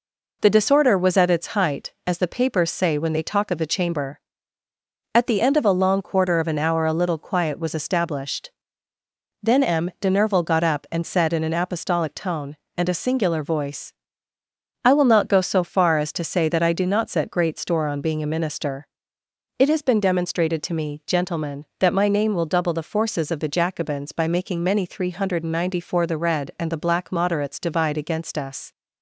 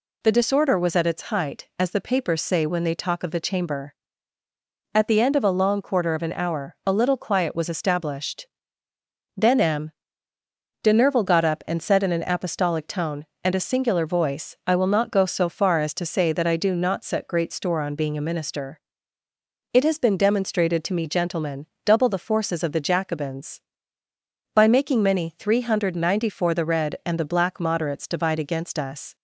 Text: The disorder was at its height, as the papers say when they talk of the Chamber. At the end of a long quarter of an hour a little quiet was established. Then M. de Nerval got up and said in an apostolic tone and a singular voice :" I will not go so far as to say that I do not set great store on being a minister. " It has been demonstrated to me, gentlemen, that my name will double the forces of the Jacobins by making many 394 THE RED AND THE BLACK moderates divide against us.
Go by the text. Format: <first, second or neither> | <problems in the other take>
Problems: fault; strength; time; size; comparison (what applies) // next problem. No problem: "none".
first | pauses between "M" and "de"; noticeable; at 9.9 s; 0.92 s long // skips "that my name will"; at 21.7 s